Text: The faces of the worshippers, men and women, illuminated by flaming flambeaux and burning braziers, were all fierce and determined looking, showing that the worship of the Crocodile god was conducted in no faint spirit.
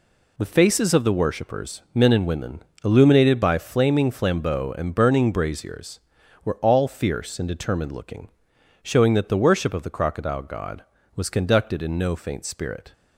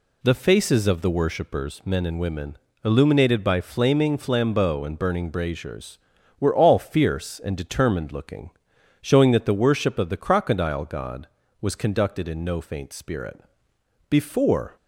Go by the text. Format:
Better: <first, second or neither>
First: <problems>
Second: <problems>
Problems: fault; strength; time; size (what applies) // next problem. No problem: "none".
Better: first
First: none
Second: goes on to say "Before"; noticeable; from 14.0 s on; 0.66 s long